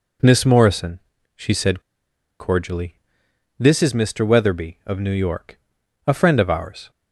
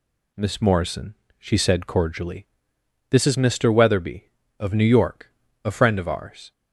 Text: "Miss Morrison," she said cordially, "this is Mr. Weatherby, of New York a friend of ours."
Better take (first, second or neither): second